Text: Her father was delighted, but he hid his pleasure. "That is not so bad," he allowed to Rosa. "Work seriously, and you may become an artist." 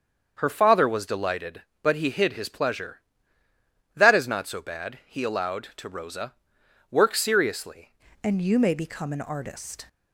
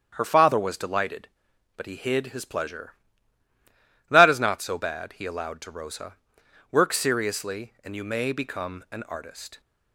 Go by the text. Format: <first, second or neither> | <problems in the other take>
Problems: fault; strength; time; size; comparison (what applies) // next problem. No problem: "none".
second | starts louder than the rest; until 1.3 s; 7 dB; strong in the second // changes voice at "and"; from 8.2 s on; 1.6 s long